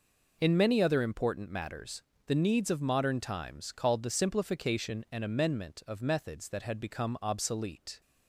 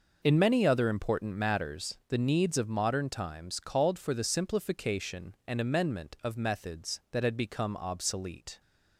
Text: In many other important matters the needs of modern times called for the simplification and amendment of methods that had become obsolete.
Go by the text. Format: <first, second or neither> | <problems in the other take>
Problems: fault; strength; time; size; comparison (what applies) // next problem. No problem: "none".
second | pauses between "matters" and "the"; slight; at 2.0 s; 0.24 s long // skips "for"; at 4.0 s